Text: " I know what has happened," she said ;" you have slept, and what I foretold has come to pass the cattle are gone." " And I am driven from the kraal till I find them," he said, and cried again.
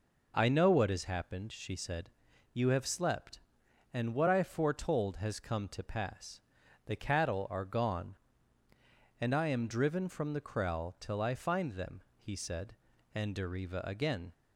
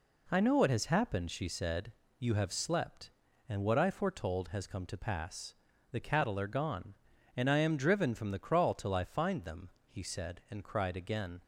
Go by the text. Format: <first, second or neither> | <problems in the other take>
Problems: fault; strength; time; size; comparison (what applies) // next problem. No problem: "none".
second | pauses between "pass" and "the"; noticeable; at 6.3 s; 0.46 s long; also in the second // says "deriva" for "cried"; at 13.3 s